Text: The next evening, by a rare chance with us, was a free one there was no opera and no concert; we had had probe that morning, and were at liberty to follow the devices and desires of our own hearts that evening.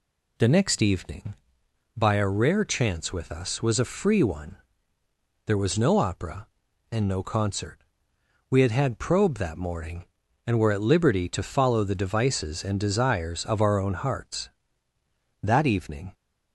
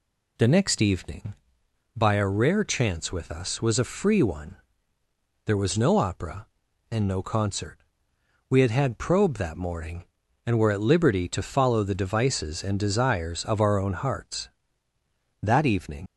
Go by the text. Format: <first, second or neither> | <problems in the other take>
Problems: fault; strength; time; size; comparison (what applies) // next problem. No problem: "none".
first | pauses between "one" and "there"; noticeable; at 4.5 s; 0.88 s long; noticeable in the first // leaves "evening" unfinished; at 16.0 s; 65 ms